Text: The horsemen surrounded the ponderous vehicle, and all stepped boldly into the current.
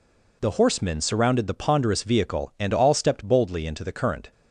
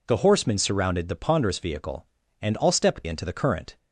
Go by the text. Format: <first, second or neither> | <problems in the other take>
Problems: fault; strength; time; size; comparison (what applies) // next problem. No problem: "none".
first | skips "boldly"; at 3.0 s